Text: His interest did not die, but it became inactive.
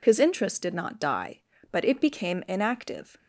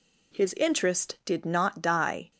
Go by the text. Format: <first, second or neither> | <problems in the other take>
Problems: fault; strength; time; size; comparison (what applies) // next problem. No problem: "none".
first | stops before "but it became inactive"; at 2.3 s